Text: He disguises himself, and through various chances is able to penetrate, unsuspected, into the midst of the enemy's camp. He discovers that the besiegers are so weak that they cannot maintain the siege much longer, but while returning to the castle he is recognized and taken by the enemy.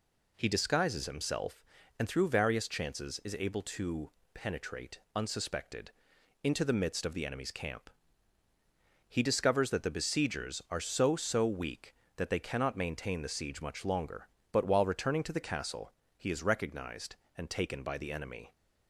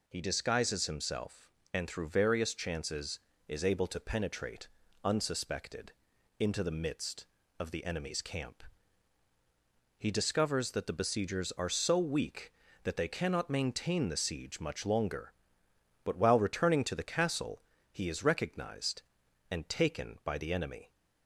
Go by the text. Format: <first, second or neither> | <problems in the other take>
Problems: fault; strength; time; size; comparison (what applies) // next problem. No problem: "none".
second | pauses between "to" and "penetrate"; slight; at 4.1 s; 0.22 s long // says "so" twice; at 11.1 s // pauses between "castle" and "he"; slight; at 15.9 s; 0.26 s long; slight in the second